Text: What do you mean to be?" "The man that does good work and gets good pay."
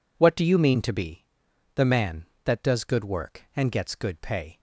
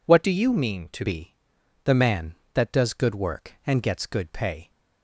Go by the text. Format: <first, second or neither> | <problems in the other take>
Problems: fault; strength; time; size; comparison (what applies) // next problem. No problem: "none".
first | changes voice from "do" to "to"; from 0.2 to 1.0 s; 0.8 s long